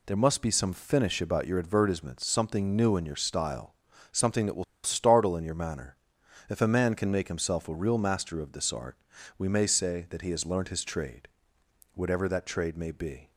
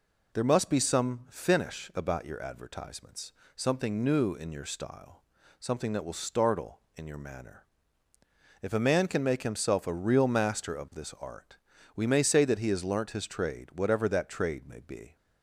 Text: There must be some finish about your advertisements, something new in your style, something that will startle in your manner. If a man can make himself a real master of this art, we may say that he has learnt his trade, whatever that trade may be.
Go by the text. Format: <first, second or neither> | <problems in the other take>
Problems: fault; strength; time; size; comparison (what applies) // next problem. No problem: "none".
second | pauses between "will" and "startle"; slight; at 4.6 s; 0.20 s long